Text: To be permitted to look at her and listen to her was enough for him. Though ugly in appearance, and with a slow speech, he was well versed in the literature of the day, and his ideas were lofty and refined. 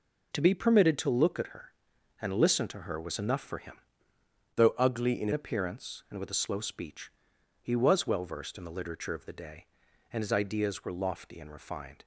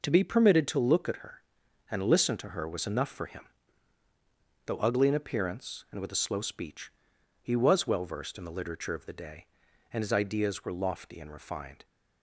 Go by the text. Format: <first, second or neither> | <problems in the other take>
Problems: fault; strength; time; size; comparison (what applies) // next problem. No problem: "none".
second | changes voice from "Though" to "in"; from 4.5 to 5.3 s; 0.8 s long